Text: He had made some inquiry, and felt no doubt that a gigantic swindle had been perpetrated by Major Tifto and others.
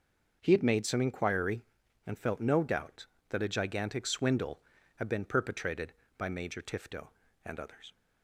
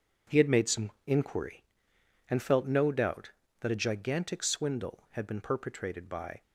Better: first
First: none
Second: stops before "Major Tifto and others"; at 6.4 s

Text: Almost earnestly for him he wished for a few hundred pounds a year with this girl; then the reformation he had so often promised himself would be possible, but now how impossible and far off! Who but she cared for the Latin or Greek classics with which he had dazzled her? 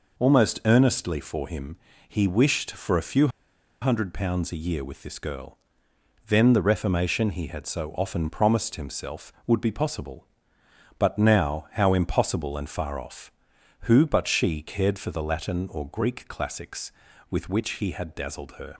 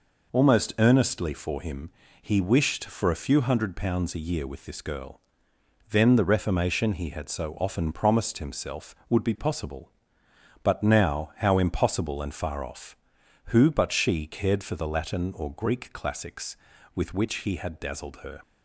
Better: second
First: pauses between "him" and "he"; slight; at 1.7 s; 0.32 s long // pauses between "few" and "hundred"; noticeable; at 3.2 s; 0.53 s long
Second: pauses between "him" and "he"; slight; at 1.8 s; 0.32 s long

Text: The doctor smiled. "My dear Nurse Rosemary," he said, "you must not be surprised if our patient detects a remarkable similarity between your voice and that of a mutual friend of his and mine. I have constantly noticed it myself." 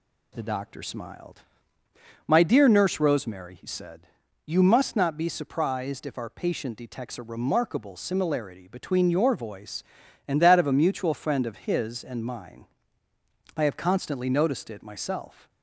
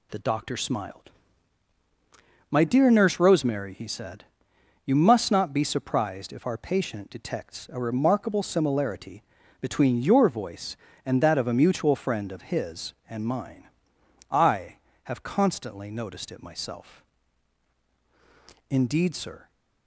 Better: first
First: none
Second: pauses between "similarity" and "between"; at 9.2 s; 0.38 s long // goes on to say "Indeed sir"; noticeable; from 18.6 s on; 0.82 s long

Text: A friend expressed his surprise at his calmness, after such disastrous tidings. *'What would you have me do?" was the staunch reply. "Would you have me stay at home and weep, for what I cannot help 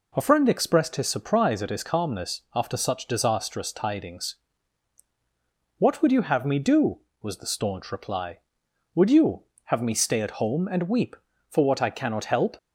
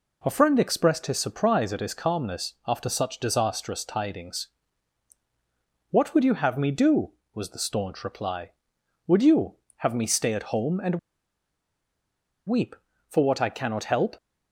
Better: first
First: none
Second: pauses between "and" and "weep"; strong; at 10.9 s; 1.4 s long

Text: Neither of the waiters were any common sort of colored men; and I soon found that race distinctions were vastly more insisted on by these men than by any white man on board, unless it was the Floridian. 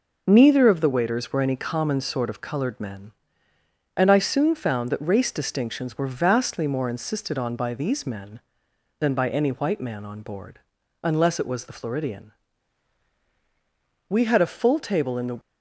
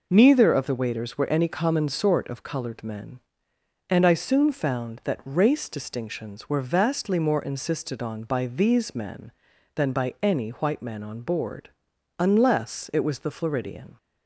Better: second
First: goes on to say "We had a full table in the"; noticeable; from 14.0 s on; 1.3 s long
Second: none

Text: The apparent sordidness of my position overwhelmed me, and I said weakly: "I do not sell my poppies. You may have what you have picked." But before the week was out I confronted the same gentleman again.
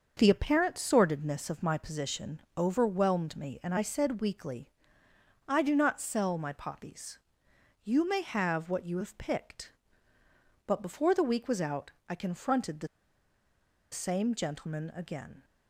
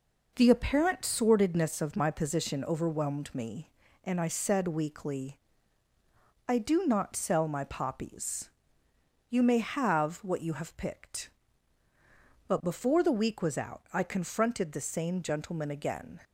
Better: second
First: starts louder than the rest; until 1.1 s; 6.5 dB // pauses between "position" and "overwhelmed"; slight; at 2.3 s; 0.16 s long // pauses between "out" and "I"; slight; at 11.9 s; 0.16 s long // pauses between "the" and "same"; at 12.8 s; 1.0 s long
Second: none

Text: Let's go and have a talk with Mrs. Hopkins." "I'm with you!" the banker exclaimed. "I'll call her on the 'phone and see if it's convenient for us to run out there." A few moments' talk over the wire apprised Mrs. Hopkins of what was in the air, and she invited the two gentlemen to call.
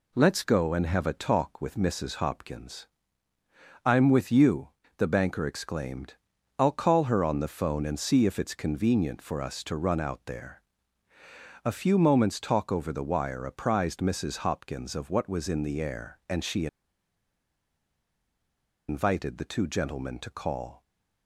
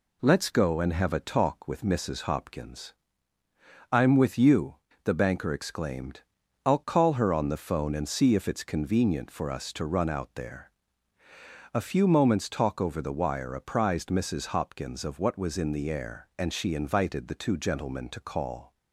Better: second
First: pauses between "she" and "invited"; strong; at 16.6 s; 2.2 s long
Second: none

